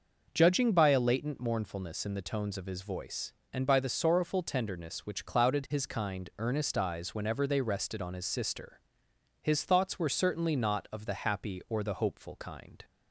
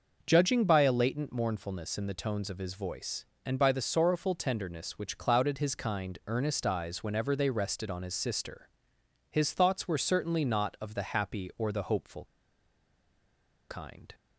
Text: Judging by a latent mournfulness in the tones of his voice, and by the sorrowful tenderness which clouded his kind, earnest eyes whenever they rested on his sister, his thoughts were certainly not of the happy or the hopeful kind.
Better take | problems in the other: first | starts louder than the rest; noticeable; until 1.2 s; 6 dB; noticeable in the first // pauses between "hopeful" and "kind"; strong; at 12.2 s; 1.4 s long

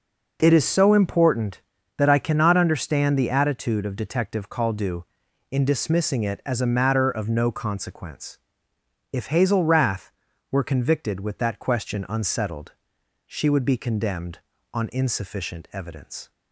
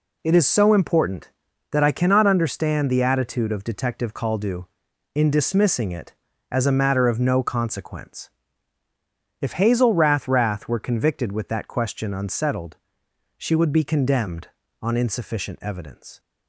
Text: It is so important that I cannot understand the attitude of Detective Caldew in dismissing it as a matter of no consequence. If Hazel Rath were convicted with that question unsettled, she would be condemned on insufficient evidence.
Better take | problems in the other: first | says "Rath" twice; at 10.2 s

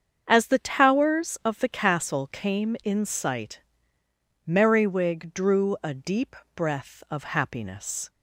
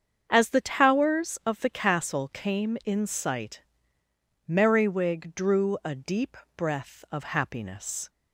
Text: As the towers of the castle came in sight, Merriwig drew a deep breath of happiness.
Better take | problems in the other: neither | starts louder than the rest; strong; the same in both // pauses between "deep" and "breath"; slight; the same in both

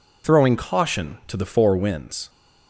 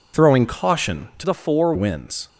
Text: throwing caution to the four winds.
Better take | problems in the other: first | changes voice from "the" to "four"; from 1.2 to 1.7 s; 0.5 s long

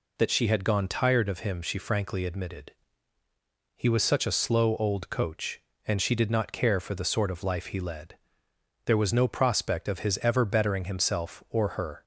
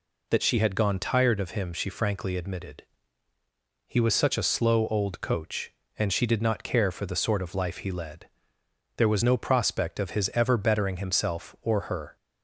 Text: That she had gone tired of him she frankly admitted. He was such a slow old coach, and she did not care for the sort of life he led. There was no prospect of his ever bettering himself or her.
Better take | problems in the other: neither | none

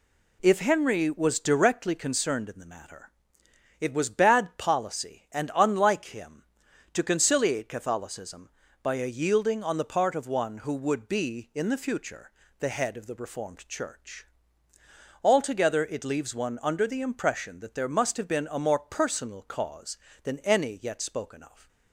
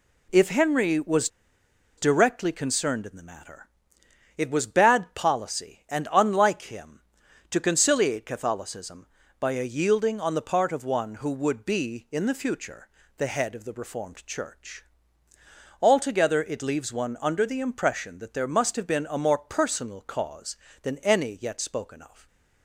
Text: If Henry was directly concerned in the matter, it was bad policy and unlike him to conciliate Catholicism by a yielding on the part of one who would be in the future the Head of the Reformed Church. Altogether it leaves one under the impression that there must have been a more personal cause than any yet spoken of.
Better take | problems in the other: first | pauses between "was" and "directly"; noticeable; at 1.2 s; 0.70 s long // pauses between "future" and "the"; slight; at 12.8 s; 0.32 s long; slight in the first

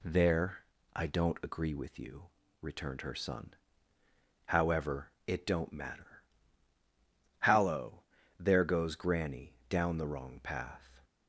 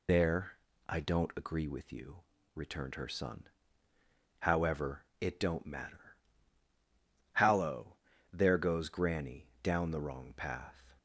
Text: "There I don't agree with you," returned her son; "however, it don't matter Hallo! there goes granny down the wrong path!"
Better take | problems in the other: first | loses the start of "There"; at 0.0 s; 145 ms // pauses between "There" and "I"; slight; at 0.5 s; 0.32 s long; slight in the first // pauses between "matter" and "Hallo"; at 6.1 s; 1.1 s long; also in the first // pauses between "granny" and "down"; slight; at 9.4 s; 0.16 s long; slight in the first

